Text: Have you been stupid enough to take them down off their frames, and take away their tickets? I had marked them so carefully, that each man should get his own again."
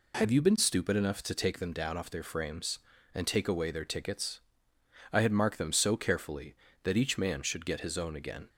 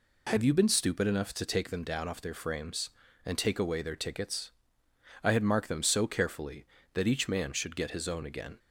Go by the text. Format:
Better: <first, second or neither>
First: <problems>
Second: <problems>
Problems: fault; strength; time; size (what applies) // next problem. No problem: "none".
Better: neither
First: none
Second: none